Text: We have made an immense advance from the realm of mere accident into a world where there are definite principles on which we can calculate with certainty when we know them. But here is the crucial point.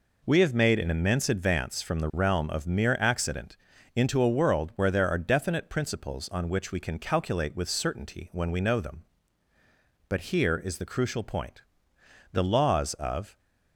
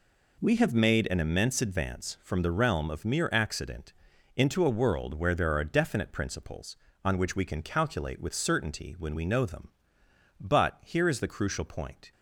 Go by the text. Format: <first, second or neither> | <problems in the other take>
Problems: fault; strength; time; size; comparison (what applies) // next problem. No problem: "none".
second | pauses between "accident" and "into"; at 3.5 s; 0.38 s long; noticeable in the second // goes on to say "The laws of"; noticeable; from 12.3 s on; 1.0 s long